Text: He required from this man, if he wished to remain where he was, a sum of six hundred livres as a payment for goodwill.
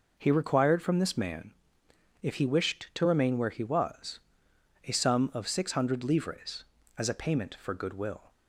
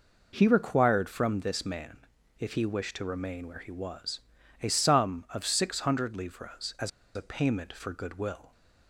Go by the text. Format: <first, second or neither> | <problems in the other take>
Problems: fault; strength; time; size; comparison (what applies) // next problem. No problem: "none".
first | pauses between "as" and "a"; slight; at 6.8 s; 0.25 s long